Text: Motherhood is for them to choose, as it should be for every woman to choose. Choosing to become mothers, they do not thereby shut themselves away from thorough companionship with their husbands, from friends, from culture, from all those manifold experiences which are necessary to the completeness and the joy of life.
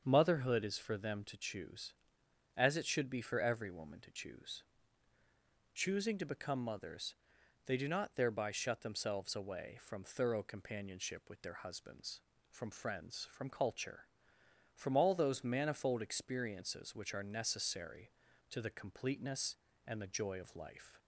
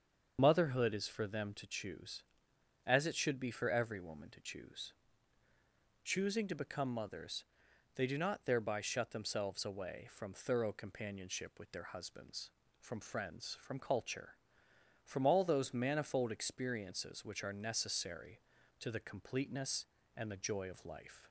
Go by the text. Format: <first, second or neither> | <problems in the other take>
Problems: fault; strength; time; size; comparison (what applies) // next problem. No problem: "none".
first | loses the start of "Motherhood"; at 0.3 s; 50 ms // starts louder than the rest; until 1.3 s; 7 dB; also in the first